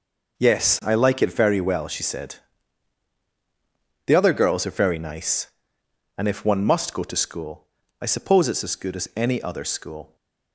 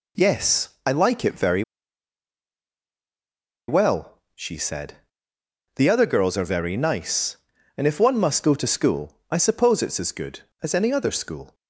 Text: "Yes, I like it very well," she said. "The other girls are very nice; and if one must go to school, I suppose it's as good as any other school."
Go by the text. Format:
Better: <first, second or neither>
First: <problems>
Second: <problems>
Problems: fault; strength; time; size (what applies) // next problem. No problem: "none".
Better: first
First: none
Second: pauses between "very" and "well"; strong; at 1.6 s; 2.0 s long